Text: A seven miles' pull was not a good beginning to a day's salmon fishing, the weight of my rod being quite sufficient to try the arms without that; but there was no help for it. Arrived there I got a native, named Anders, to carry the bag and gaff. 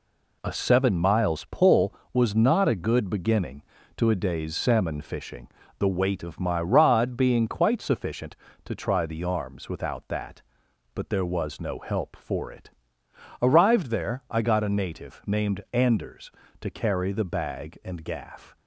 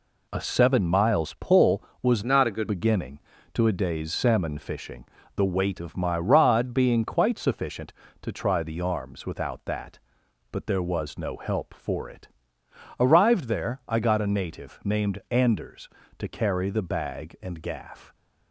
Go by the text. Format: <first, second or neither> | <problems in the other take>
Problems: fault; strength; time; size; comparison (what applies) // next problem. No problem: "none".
first | changes voice from "not" to "good"; from 2.2 to 2.6 s; 0.4 s long